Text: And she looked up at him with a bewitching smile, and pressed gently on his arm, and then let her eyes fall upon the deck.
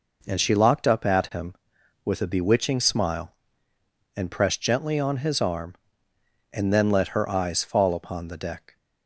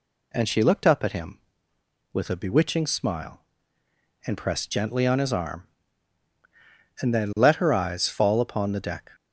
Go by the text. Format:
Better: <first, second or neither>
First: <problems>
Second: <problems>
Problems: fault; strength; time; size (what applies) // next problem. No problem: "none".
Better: second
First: says "locked" for "looked"; at 0.5 s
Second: none